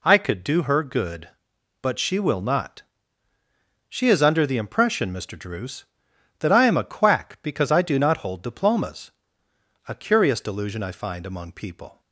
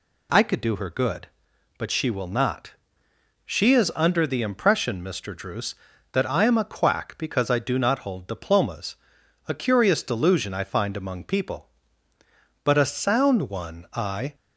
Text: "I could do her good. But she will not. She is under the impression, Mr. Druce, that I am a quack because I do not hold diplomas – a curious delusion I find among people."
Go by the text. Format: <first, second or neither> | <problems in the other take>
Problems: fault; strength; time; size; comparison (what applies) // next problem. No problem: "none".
first | goes on to say "But a sound one I"; strong; from 12.6 s on; 1.7 s long